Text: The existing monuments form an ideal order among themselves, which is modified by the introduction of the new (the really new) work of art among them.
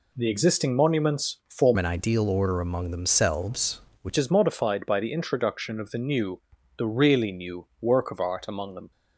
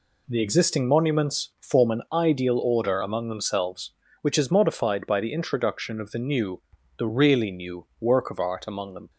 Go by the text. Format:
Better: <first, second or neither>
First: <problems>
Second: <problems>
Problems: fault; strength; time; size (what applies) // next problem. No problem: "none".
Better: second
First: changes voice from "an" to "which"; from 1.7 to 4.1 s; 2.4 s long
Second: none